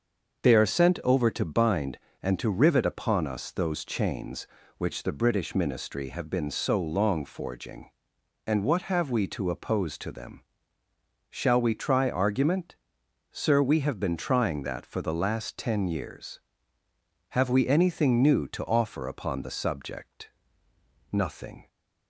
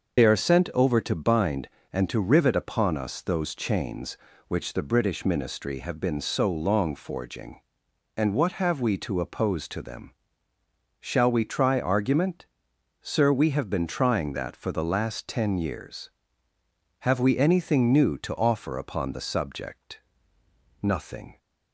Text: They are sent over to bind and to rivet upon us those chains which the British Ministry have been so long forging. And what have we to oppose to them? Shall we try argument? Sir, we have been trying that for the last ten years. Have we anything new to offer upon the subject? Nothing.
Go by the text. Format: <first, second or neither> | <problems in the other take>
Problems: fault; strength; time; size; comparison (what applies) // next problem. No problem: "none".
first | loses the start of "They"; at 0.1 s; 60 ms // starts louder than the rest; until 1.2 s; 6 dB; also in the first